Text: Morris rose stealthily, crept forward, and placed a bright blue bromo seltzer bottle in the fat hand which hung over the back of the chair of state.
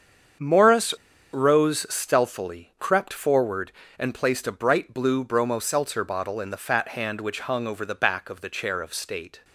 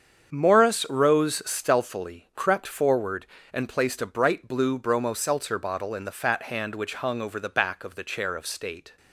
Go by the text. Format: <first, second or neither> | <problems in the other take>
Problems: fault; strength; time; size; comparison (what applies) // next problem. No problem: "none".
second | starts louder than the rest; strong; until 1.7 s; 7.5 dB; strong in the second // pauses between "Morris" and "rose"; at 0.9 s; 0.38 s long